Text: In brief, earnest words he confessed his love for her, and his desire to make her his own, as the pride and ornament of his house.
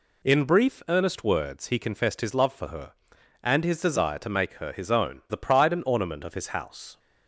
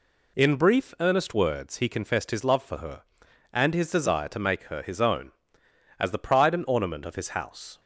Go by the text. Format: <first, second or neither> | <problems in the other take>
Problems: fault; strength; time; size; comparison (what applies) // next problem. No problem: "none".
second | skips "as"; at 5.2 s